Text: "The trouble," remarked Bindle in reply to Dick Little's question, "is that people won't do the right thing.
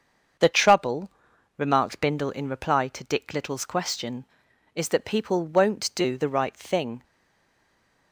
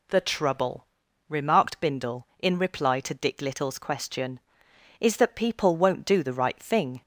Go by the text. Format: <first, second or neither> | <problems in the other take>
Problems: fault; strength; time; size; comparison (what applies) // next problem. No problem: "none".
second | starts louder than the rest; until 1.8 s; 7 dB // stays silent after the last word; from 7.0 s on; 1.1 s long